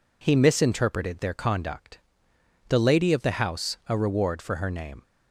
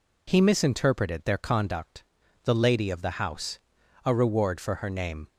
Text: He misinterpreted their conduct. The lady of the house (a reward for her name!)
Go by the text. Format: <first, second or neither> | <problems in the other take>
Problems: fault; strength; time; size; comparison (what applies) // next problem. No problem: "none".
neither | none